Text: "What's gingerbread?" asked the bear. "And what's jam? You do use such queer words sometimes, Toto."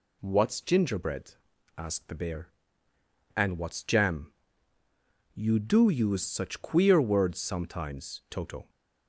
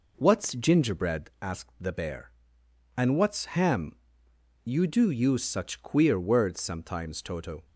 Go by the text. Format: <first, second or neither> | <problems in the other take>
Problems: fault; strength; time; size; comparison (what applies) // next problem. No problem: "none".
first | says "ham" for "jam"; at 3.4 s